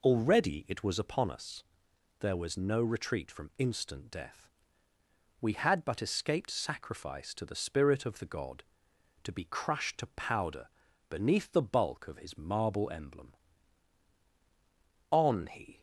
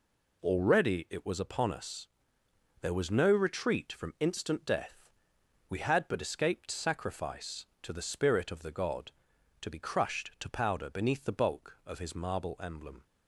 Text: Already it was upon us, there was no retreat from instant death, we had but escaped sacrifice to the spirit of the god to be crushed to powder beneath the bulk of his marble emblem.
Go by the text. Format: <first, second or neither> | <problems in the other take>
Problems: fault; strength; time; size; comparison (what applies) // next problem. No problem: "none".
second | pauses between "powder" and "beneath"; at 10.6 s; 0.42 s long // goes on to say "On he"; noticeable; from 15.1 s on; 0.70 s long